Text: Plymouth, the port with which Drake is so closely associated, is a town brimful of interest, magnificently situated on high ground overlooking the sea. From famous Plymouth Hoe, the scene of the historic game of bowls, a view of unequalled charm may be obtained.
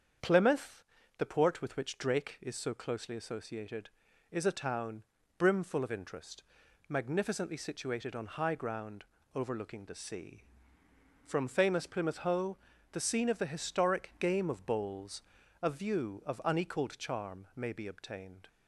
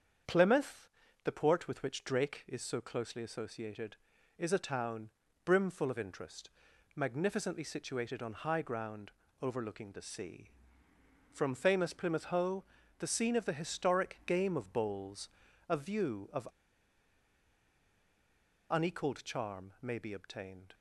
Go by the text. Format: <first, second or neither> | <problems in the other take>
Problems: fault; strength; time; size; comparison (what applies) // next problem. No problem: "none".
first | starts louder than the rest; strong; until 1.6 s; 7.5 dB; strong in the first // pauses between "town" and "brimful"; slight; at 5.1 s; 0.34 s long; slight in the first // pauses between "ground" and "overlooking"; slight; at 9.1 s; 0.28 s long; slight in the first // pauses between "of" and "unequalled"; strong; at 16.4 s; 2.2 s long